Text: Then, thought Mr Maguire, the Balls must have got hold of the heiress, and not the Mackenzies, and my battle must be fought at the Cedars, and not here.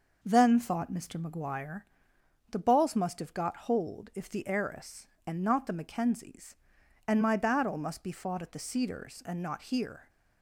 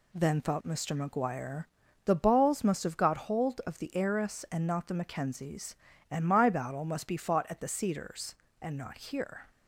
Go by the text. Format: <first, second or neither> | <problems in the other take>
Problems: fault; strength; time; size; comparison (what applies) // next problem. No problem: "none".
second | says "if" for "of"; at 4.1 s